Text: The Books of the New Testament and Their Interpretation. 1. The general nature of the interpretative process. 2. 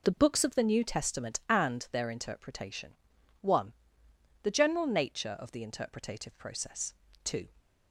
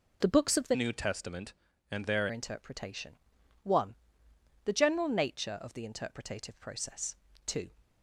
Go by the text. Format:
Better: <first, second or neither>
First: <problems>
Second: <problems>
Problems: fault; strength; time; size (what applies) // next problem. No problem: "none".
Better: first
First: none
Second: changes voice from "New" to "Their"; from 0.7 to 2.2 s; 1.5 s long